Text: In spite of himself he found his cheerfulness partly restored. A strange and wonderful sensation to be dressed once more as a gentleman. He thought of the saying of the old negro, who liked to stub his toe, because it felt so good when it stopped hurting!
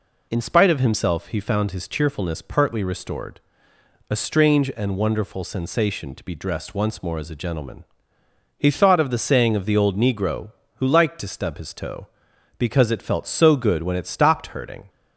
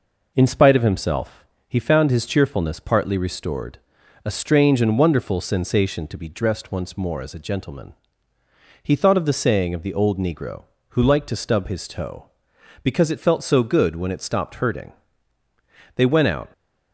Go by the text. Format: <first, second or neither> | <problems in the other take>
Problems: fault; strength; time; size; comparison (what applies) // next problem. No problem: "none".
first | pauses between "himself" and "he"; slight; at 1.4 s; 0.24 s long // goes on to say "They went out"; from 15.9 s on; 0.56 s long